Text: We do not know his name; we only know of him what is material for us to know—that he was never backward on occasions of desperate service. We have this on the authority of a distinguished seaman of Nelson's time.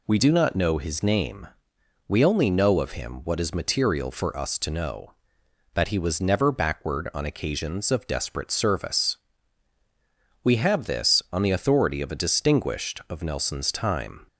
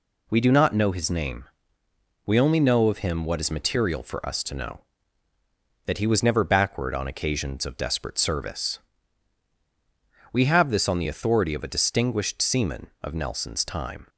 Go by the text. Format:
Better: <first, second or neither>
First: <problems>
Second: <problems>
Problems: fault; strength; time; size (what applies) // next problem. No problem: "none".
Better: second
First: skips "seaman"; at 13.0 s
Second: none